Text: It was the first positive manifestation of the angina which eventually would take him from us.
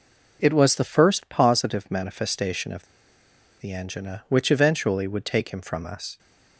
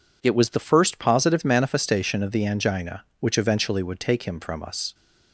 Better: second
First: pauses between "of" and "the"; noticeable; at 2.8 s; 0.73 s long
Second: none

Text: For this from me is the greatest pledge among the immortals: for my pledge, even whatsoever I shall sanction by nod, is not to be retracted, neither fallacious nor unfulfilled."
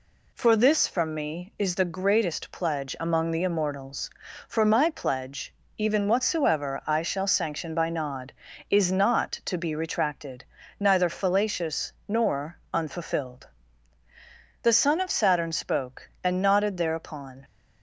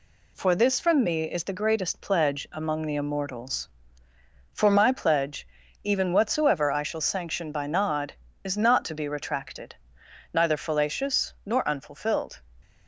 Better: second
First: pauses between "fallacious" and "nor"; slight; at 11.9 s; 0.16 s long // pauses between "nor" and "unfulfilled"; slight; at 12.5 s; 0.16 s long // goes on to say "The son of Saturn spoke and nodded thereupon"; strong; from 14.6 s on; 2.8 s long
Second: none

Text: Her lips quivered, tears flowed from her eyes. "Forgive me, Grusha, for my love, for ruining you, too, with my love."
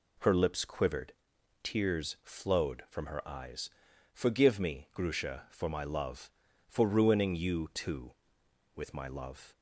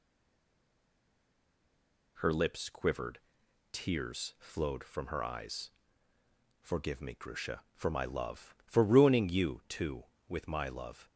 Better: first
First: none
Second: stays silent before the first word; until 2.1 s; 2.1 s long

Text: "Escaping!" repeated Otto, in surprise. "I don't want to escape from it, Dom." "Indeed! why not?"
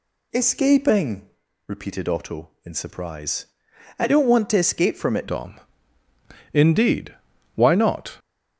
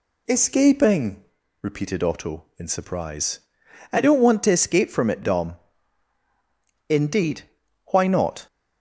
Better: second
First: changes voice at "Dom"; from 5.2 s on; 2.9 s long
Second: none

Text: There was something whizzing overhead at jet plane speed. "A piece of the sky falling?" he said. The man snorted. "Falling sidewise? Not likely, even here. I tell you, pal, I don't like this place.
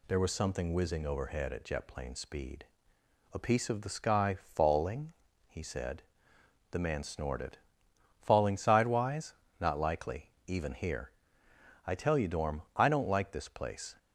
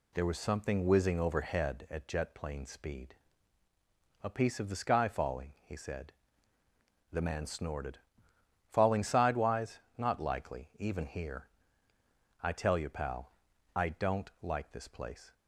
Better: second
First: says "dorm" for "pal"; at 12.2 s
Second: none

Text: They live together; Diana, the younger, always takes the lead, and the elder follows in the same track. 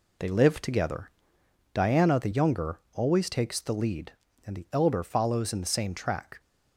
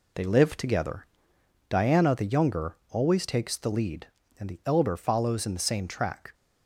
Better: neither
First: none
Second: none

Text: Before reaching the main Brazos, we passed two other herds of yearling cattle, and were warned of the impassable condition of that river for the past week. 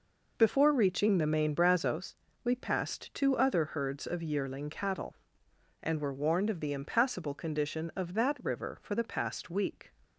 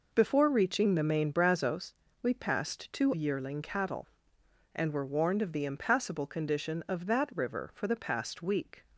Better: first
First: none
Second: skips "other herds of"; at 3.1 s

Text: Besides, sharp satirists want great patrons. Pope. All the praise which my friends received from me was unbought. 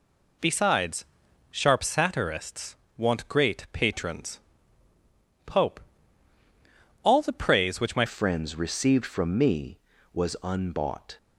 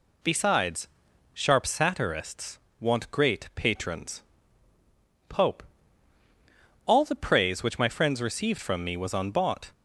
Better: second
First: pauses between "satirists" and "want"; slight; at 2.7 s; 0.20 s long // changes voice at "friends"; from 8.0 s on; 3.1 s long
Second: pauses between "satirists" and "want"; slight; at 2.5 s; 0.20 s long

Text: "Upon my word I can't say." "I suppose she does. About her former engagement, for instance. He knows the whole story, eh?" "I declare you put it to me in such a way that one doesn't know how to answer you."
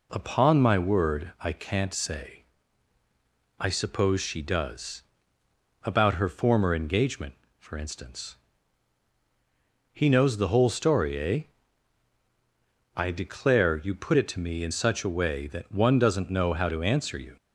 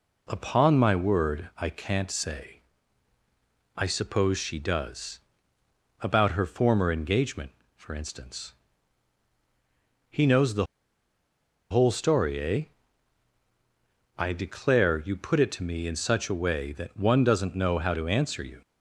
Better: first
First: none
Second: pauses between "the" and "whole"; at 10.6 s; 1.0 s long

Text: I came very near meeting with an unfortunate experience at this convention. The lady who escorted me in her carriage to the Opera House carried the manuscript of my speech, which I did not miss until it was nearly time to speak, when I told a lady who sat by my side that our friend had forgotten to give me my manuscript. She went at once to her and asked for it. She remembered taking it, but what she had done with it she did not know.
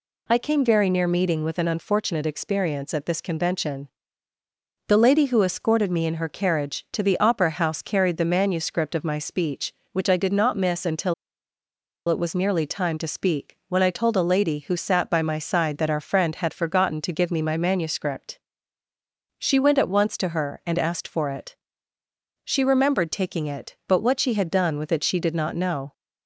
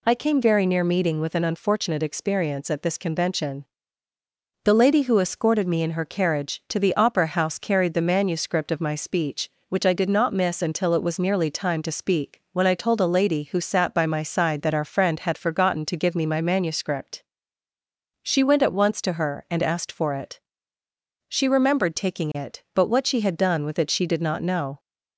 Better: second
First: pauses between "until" and "it"; noticeable; at 11.1 s; 0.94 s long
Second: none

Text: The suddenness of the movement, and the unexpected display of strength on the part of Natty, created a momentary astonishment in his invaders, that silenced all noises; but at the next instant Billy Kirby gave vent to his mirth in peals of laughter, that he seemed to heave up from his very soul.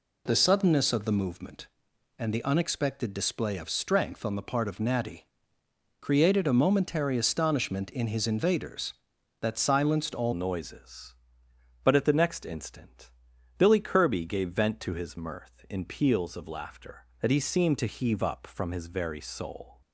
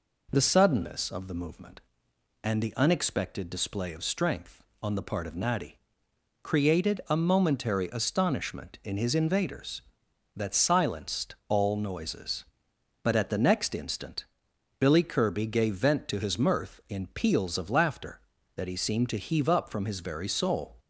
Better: second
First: changes voice at "noises"; from 10.3 s on; 9.5 s long // pauses between "instant" and "Billy"; noticeable; at 13.1 s; 0.48 s long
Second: pauses between "instant" and "Billy"; noticeable; at 14.2 s; 0.54 s long

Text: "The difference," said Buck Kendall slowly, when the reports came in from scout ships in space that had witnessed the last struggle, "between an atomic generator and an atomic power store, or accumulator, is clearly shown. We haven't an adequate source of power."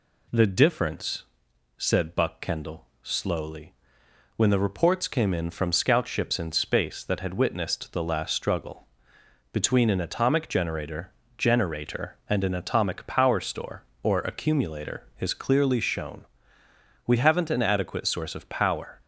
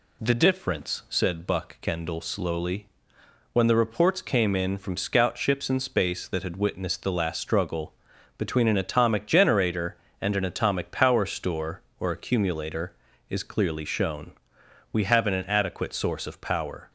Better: second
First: pauses between "Kendall" and "slowly"; slight; at 2.8 s; 0.16 s long // says "generator" twice; at 11.3 s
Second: none

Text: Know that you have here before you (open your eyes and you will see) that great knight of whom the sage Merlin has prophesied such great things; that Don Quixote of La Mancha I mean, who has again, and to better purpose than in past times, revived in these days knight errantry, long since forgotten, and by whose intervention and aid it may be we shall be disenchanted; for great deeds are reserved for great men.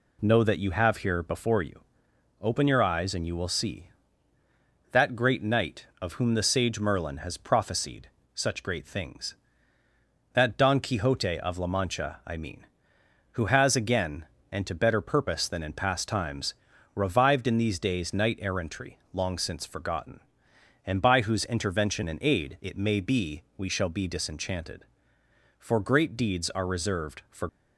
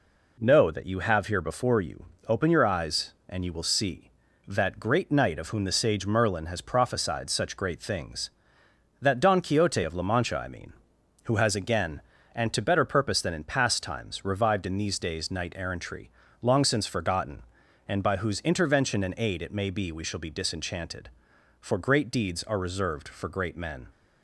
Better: second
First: pauses between "prophesied" and "such"; slight; at 8.0 s; 0.24 s long // stops before "great men"; at 27.4 s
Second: none

